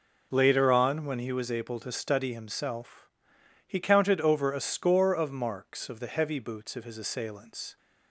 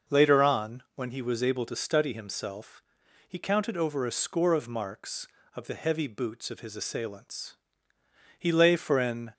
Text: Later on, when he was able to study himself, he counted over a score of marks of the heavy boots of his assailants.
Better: first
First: none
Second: goes on to say "He lay for an"; noticeable; from 8.3 s on; 0.94 s long

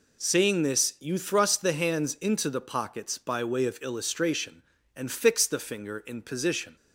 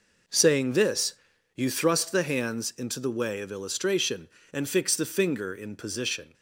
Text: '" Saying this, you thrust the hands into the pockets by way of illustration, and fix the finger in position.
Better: first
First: none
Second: skips "pockets by"; at 3.0 s

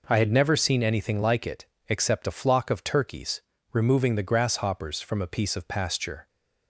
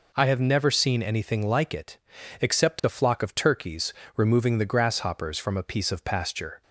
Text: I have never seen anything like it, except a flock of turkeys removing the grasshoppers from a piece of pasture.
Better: second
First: says "had" for "have"; at 0.1 s // pauses between "turkeys" and "removing"; slight; at 3.4 s; 0.30 s long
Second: pauses between "turkeys" and "removing"; slight; at 3.9 s; 0.24 s long

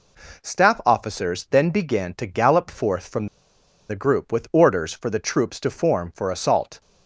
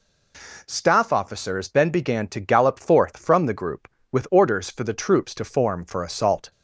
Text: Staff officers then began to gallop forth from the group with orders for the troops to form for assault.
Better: second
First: pauses between "from" and "the"; noticeable; at 3.2 s; 0.62 s long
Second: none

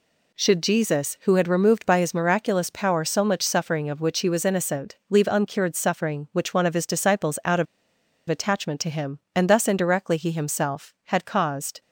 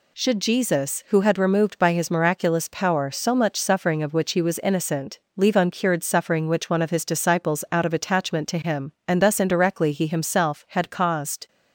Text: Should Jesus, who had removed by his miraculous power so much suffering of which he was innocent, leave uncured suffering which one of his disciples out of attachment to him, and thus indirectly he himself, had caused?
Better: second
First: pauses between "of" and "attachment"; noticeable; at 7.6 s; 0.64 s long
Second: none

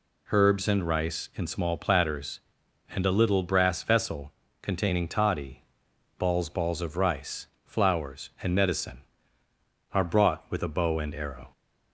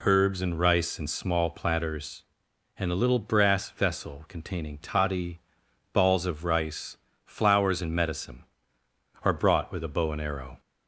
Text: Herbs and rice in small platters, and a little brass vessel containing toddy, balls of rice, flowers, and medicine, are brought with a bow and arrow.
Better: second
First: pauses between "vessel" and "containing"; slight; at 4.3 s; 0.28 s long // says "balls" twice; at 6.4 s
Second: none

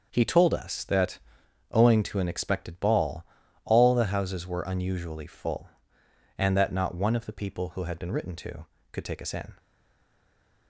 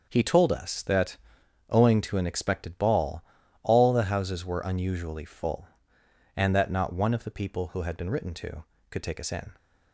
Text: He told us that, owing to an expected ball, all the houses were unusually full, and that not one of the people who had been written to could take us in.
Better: second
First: starts louder than the rest; until 1.1 s; 6.5 dB // stays silent after the last word; from 9.5 s on; 1.1 s long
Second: starts louder than the rest; until 1.1 s; 6.5 dB

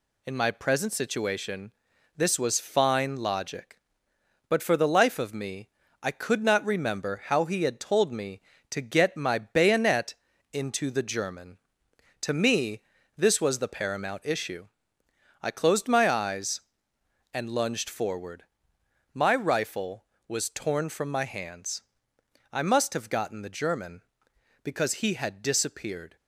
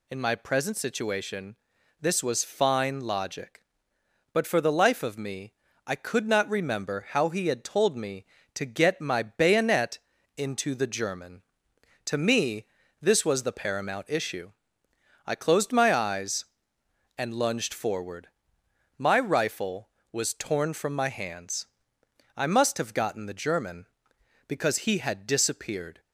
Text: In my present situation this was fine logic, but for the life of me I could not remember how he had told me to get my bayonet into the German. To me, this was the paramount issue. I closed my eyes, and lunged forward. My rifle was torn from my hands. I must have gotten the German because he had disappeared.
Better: second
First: gets quieter; slight; throughout; 3 dB // pauses between "situation" and "this"; at 1.7 s; 0.44 s long // pauses between "me" and "I"; slight; at 5.6 s; 0.34 s long // pauses between "bayonet" and "into"; at 10.1 s; 0.38 s long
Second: pauses between "situation" and "this"; at 1.5 s; 0.44 s long // pauses between "me" and "I"; slight; at 5.5 s; 0.34 s long // pauses between "bayonet" and "into"; at 9.9 s; 0.38 s long

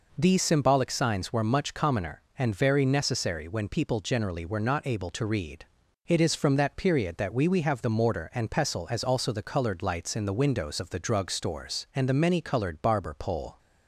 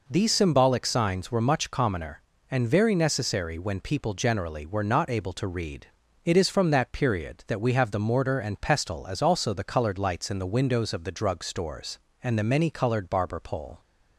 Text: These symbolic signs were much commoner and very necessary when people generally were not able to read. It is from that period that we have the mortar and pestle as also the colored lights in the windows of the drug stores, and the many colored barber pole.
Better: second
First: says "we" twice; at 7.4 s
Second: none

